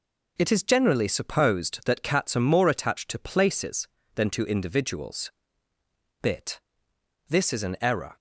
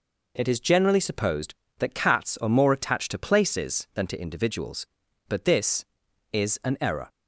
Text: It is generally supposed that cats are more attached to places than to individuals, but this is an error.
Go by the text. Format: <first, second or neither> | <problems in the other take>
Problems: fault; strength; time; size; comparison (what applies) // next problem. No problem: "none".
second | says "bit" for "but"; at 6.2 s